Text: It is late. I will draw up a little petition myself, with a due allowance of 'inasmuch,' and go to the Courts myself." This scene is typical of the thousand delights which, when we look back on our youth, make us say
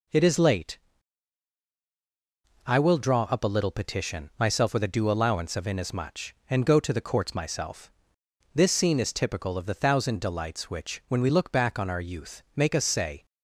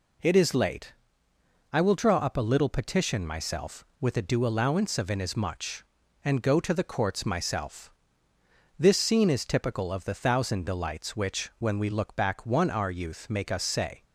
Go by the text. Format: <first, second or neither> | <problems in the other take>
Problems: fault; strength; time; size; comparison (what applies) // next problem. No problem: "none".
first | says "one" for "on"; at 12.4 s